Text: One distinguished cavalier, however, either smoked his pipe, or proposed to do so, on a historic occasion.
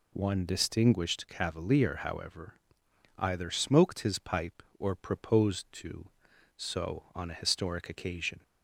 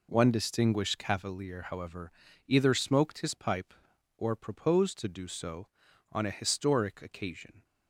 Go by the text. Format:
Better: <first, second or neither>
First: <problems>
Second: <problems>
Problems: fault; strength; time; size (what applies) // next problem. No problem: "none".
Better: second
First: skips "do"; at 6.3 s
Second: none